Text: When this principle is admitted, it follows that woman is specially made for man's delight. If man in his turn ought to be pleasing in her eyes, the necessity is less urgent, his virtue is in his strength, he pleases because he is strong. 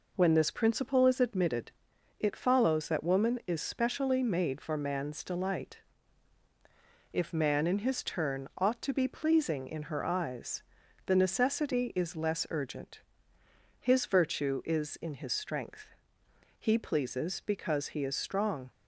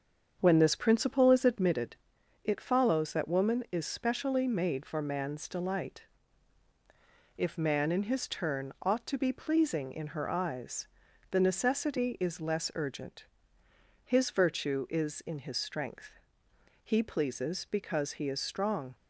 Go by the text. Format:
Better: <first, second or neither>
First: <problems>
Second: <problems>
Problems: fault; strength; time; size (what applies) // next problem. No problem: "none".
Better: first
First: none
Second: starts louder than the rest; strong; until 1.8 s; 7 dB